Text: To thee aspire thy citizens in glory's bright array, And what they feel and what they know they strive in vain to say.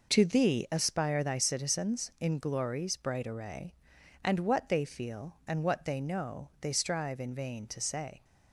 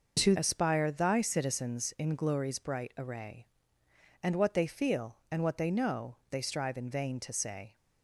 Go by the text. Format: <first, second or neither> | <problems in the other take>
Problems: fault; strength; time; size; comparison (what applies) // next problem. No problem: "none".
first | skips "thee"; at 0.3 s // pauses between "know" and "they"; slight; at 6.1 s; 0.16 s long